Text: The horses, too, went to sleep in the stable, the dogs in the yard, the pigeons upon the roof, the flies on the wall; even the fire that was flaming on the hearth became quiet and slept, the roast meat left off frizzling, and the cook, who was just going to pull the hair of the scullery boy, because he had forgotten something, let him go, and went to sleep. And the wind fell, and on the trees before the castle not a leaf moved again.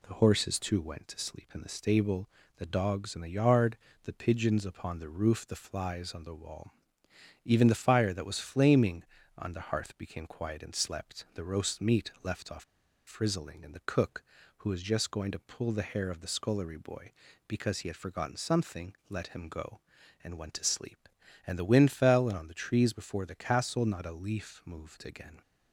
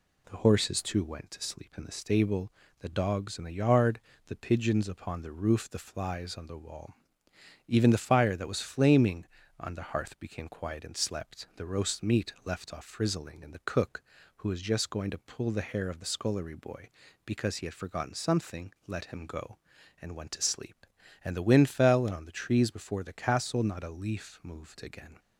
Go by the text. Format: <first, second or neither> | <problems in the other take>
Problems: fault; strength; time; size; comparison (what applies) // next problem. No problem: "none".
second | pauses between "off" and "frizzling"; at 12.6 s; 0.42 s long